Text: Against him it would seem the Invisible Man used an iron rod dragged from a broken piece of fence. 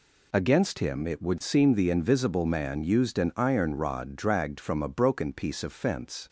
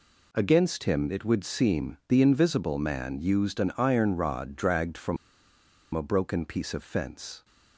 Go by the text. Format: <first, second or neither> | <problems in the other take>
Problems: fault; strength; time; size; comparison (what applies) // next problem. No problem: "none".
first | pauses between "from" and "a"; noticeable; at 5.1 s; 0.78 s long